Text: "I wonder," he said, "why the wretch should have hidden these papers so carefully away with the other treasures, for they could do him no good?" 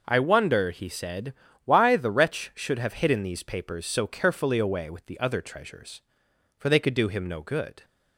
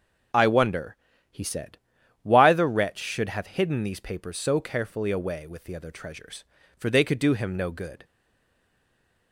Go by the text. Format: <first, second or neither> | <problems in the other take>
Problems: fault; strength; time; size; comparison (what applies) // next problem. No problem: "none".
first | starts louder than the rest; until 1.6 s; 6.5 dB // stays silent after the last word; noticeable; from 8.0 s on; 1.3 s long